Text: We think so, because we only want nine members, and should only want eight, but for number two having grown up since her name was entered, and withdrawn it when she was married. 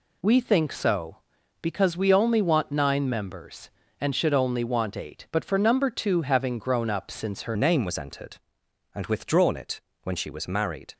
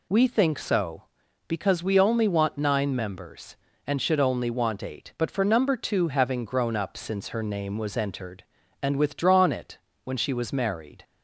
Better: second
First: changes voice at "name"; from 7.5 s on; 3.4 s long // pauses between "it" and "when"; slight; at 9.8 s; 0.22 s long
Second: pauses between "it" and "when"; slight; at 9.7 s; 0.26 s long

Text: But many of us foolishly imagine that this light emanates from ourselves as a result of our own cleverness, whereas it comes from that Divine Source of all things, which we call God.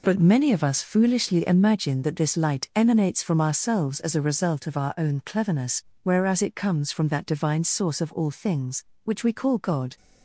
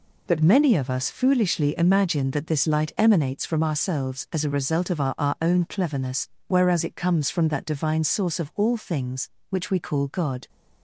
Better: first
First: none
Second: says "our" twice; at 5.1 s

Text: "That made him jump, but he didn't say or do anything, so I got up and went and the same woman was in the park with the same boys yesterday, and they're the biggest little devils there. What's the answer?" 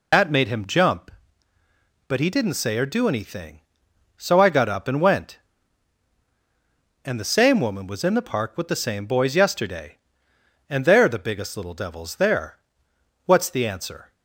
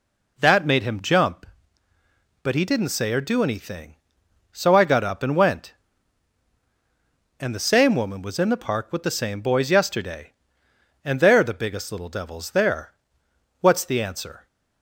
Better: second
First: loses the start of "That"; at 0.1 s; 90 ms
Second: none

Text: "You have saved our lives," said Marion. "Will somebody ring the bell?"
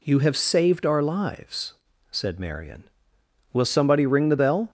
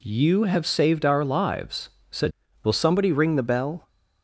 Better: first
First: none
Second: skips "Marion"; at 2.4 s

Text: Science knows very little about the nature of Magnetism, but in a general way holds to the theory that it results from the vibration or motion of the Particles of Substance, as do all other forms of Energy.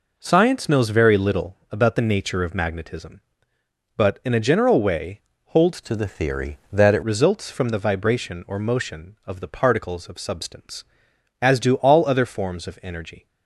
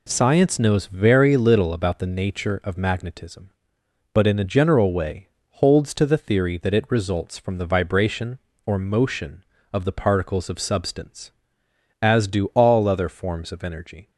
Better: second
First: pauses between "way" and "holds"; slight; at 5.2 s; 0.26 s long // changes voice from "to" to "it"; from 5.8 to 7.0 s; 1.2 s long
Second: pauses between "way" and "holds"; slight; at 5.2 s; 0.24 s long

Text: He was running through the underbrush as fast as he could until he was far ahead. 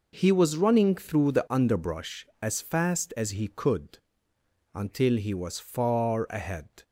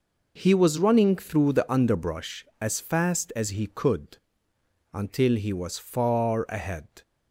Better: neither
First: pauses between "could" and "until"; noticeable; at 3.9 s; 0.76 s long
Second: pauses between "could" and "until"; noticeable; at 4.1 s; 0.76 s long

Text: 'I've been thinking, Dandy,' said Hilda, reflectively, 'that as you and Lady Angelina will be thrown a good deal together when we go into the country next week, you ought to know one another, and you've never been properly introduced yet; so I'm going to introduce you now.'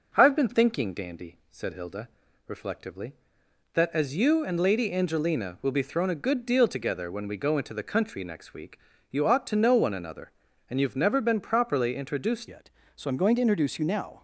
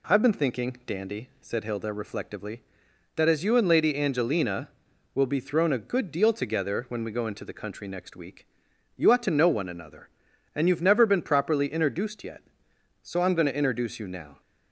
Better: second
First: changes voice at "yet"; from 12.4 s on; 1.8 s long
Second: none

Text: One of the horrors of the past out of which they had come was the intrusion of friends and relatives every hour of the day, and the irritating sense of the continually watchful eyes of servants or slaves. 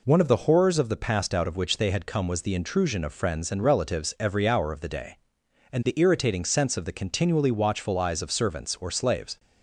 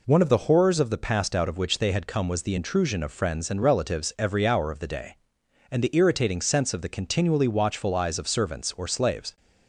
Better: neither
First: none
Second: none

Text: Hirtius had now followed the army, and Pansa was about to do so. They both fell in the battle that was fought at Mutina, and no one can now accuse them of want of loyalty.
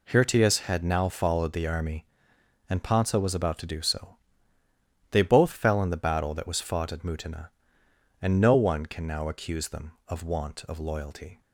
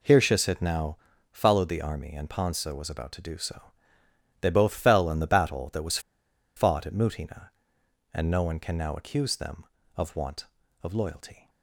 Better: first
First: none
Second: pauses between "now" and "followed"; slight; at 0.9 s; 0.34 s long // pauses between "was" and "fought"; noticeable; at 5.9 s; 0.57 s long

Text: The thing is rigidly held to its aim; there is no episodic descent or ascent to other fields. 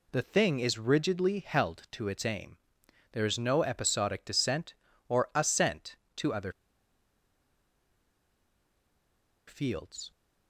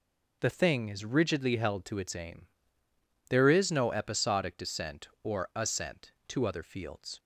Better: second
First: pauses between "other" and "fields"; strong; at 6.5 s; 2.9 s long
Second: none

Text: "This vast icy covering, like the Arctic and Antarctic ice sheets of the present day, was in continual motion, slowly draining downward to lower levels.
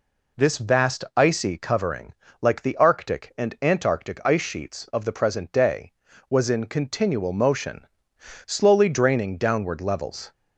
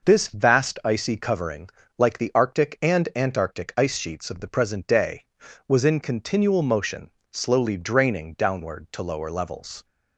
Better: second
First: skips "to lower"; at 9.8 s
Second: none

